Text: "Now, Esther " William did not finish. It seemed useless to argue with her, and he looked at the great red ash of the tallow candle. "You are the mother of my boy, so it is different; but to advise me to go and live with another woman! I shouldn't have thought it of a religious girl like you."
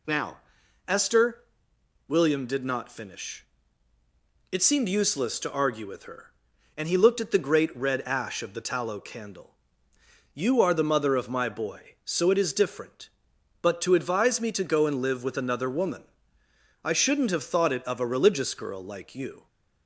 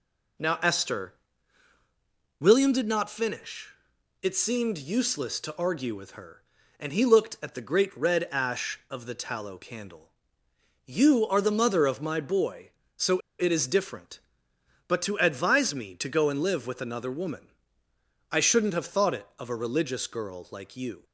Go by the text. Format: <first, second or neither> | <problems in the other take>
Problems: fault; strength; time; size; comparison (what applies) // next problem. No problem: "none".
first | pauses between "so" and "it"; slight; at 13.1 s; 0.19 s long